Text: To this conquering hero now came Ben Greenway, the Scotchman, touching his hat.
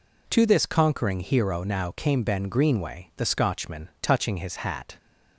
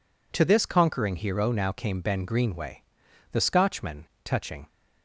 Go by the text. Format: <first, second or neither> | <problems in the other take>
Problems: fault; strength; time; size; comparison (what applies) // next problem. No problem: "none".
first | stops before "his hat"; at 4.6 s